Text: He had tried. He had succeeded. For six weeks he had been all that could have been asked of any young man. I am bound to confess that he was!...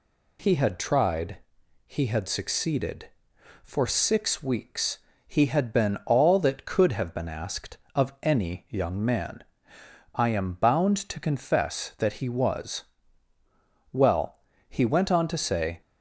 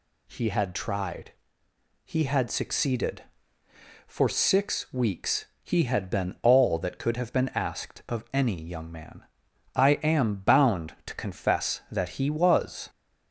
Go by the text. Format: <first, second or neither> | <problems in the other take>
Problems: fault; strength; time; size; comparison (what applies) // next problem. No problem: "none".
second | pauses between "weeks" and "he"; slight; at 4.9 s; 0.30 s long; slight in the second // goes on to say "Well he went on to say"; strong; from 13.9 s on; 1.8 s long